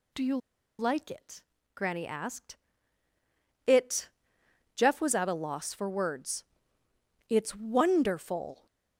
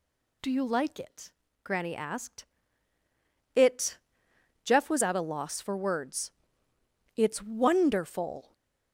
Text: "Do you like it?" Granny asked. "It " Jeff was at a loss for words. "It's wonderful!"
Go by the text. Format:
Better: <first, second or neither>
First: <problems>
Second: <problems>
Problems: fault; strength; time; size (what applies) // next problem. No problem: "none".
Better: second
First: pauses between "you" and "like"; at 0.3 s; 0.41 s long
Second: none